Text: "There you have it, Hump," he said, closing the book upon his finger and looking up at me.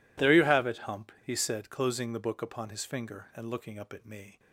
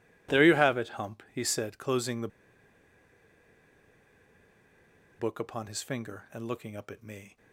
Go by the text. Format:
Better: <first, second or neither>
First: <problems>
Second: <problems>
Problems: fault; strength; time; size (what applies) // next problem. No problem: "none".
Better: first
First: none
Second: pauses between "the" and "book"; strong; at 2.2 s; 2.9 s long